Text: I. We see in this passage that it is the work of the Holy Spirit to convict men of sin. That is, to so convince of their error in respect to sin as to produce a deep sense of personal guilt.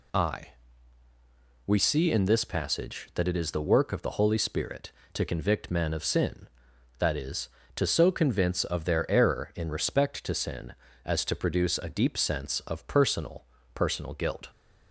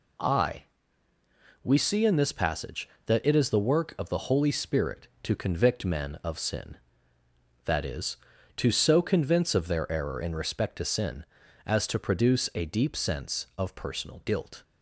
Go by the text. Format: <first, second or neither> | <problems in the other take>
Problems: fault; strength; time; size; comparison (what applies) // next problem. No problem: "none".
second | says "personal" twice; at 13.7 s